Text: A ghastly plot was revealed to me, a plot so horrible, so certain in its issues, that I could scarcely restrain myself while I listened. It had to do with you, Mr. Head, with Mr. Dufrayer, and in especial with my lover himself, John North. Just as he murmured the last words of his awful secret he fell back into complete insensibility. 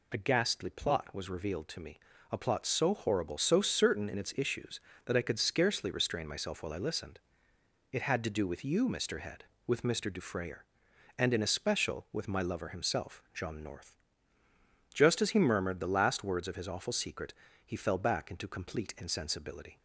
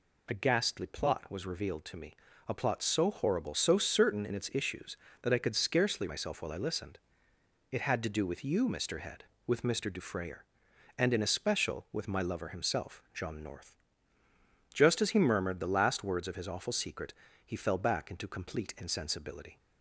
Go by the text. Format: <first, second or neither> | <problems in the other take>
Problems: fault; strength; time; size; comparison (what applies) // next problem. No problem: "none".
first | skips "restrain"; at 6.0 s // pauses between "secret" and "he"; slight; at 17.1 s; 0.30 s long; slight in the first